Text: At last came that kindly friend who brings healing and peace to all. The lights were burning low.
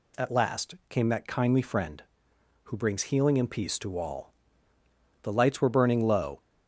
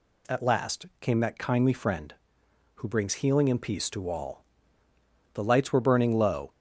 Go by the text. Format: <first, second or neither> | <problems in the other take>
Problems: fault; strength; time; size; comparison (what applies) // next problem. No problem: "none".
neither | none